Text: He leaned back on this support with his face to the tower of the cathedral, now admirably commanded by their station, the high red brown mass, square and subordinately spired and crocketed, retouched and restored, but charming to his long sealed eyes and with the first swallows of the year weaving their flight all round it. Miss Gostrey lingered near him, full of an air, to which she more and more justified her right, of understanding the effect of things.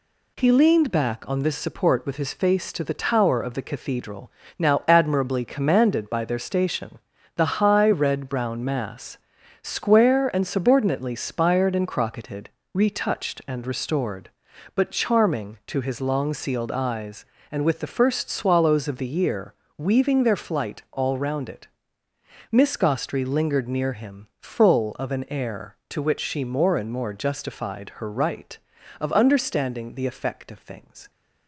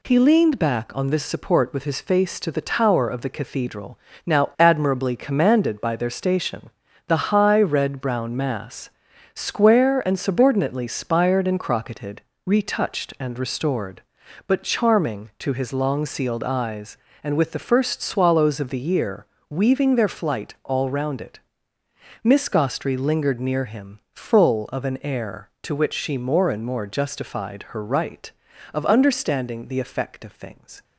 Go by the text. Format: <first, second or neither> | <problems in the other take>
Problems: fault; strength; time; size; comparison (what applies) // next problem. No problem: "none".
neither | pauses between "year" and "weaving"; slight; the same in both